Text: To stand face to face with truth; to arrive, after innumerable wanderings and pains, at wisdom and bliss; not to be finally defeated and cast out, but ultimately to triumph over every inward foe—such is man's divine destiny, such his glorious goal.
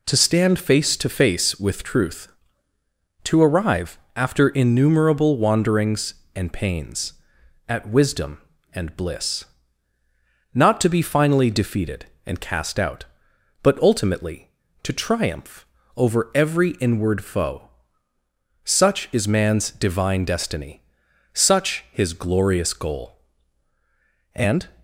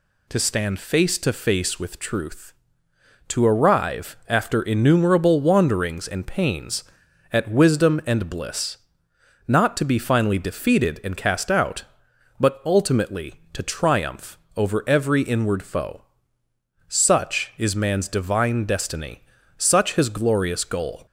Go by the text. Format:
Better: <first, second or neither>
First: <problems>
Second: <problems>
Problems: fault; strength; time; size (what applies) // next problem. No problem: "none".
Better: second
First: pauses between "triumph" and "over"; slight; at 15.6 s; 0.32 s long // goes on to say "And"; slight; from 24.3 s on; 0.36 s long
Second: pauses between "triumph" and "over"; slight; at 14.3 s; 0.16 s long